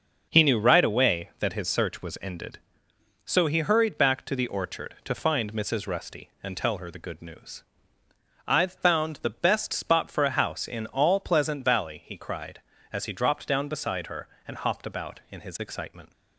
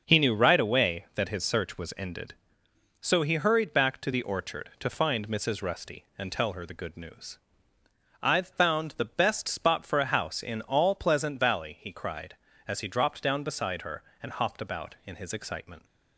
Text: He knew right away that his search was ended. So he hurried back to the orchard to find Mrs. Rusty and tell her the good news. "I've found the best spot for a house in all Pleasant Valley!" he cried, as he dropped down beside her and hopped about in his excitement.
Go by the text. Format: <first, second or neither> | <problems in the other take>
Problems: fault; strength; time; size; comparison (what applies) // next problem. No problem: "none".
neither | starts louder than the rest; the same in both